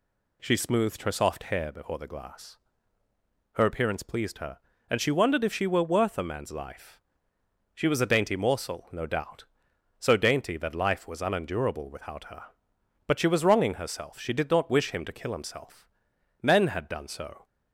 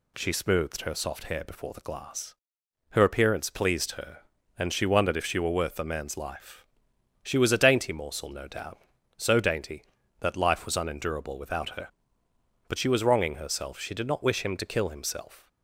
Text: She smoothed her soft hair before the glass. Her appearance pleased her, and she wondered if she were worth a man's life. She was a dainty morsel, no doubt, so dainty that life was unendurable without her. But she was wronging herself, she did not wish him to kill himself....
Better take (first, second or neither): second